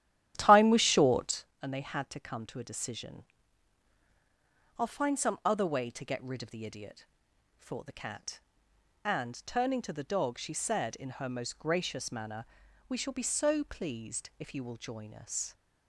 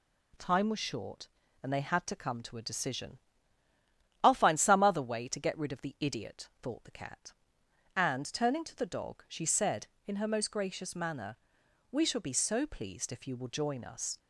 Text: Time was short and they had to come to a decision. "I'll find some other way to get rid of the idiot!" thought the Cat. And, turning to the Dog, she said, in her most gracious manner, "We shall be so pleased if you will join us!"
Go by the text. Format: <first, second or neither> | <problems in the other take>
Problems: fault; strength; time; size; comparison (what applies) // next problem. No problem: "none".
second | starts louder than the rest; strong; until 1.5 s; 12 dB